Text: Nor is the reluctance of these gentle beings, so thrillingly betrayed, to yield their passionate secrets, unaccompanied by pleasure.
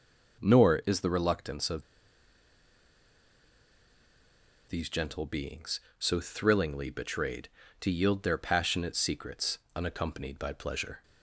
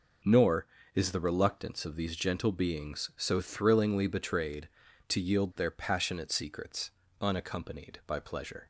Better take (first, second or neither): second